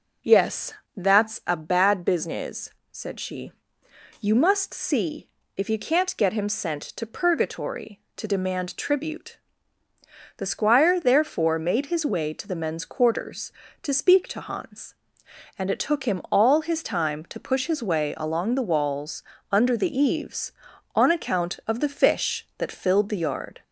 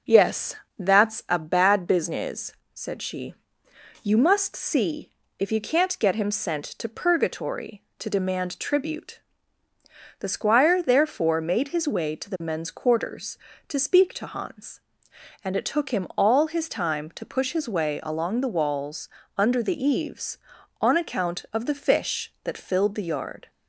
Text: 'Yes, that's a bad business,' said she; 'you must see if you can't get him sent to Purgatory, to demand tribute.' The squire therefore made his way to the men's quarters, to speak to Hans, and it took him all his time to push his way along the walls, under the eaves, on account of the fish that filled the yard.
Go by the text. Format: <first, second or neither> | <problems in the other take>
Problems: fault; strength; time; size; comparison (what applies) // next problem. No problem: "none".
second | gets louder; slight; throughout; 2 dB // pauses between "see" and "if"; slight; at 5.2 s; 0.28 s long; slight in the second